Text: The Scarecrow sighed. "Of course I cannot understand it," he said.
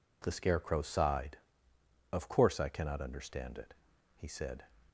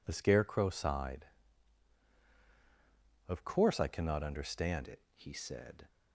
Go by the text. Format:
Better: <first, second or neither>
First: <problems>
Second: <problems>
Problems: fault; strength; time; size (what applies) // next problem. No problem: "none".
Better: first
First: none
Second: changes voice at "it"; from 4.8 s on; 1.0 s long